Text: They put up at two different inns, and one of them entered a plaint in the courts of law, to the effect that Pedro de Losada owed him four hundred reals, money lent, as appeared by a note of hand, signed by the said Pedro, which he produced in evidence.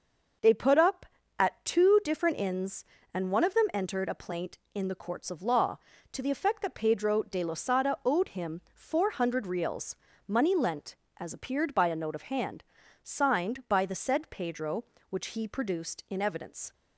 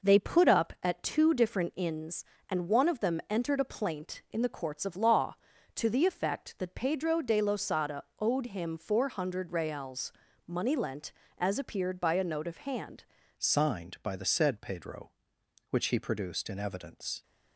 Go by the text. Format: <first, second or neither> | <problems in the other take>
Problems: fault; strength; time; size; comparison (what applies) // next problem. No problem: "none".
first | pauses between "Losada" and "owed"; slight; at 8.0 s; 0.16 s long // changes voice at "signed"; from 13.3 s on; 3.9 s long